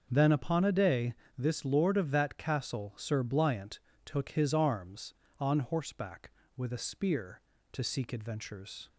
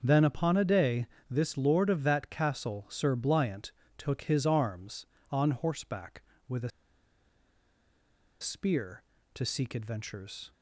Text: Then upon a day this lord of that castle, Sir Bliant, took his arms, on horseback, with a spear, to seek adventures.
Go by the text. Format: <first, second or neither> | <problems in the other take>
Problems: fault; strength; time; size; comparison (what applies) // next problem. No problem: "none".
first | starts louder than the rest; until 1.0 s; 6.5 dB; also in the first // pauses between "day" and "this"; slight; at 1.0 s; 0.22 s long; slight in the first // pauses between "a" and "spear"; strong; at 6.7 s; 1.7 s long